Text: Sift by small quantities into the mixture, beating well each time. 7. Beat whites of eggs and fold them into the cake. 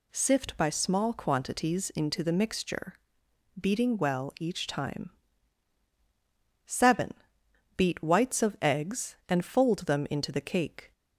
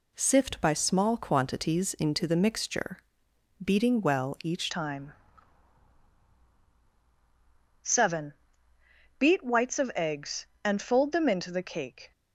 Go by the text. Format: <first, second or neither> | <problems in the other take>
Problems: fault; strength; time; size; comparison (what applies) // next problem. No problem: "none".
first | changes voice at "time"; from 4.6 s on; 7.5 s long